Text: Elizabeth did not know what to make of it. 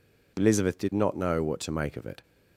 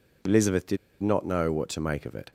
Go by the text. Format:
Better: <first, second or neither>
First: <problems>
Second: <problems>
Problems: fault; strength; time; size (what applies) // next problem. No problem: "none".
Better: first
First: none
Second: pauses between "did" and "not"; slight; at 0.7 s; 0.25 s long